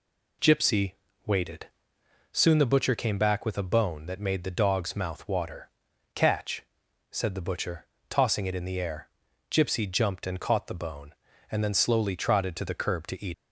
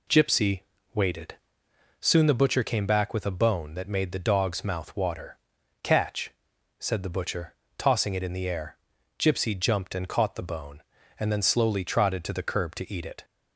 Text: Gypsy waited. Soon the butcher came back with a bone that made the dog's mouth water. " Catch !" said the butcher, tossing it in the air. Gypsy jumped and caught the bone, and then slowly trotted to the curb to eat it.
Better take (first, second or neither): second